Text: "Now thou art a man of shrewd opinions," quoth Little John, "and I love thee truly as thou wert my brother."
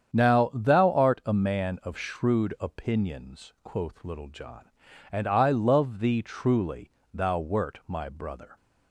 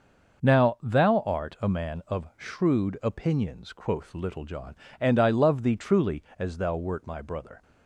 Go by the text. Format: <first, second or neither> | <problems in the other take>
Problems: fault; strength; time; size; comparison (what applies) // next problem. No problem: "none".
second | starts louder than the rest; strong; until 1.2 s; 8 dB // skips "as"; at 7.0 s